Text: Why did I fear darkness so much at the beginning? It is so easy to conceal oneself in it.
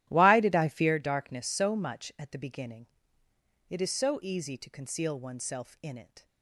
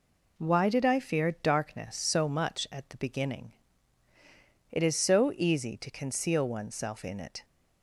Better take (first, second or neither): second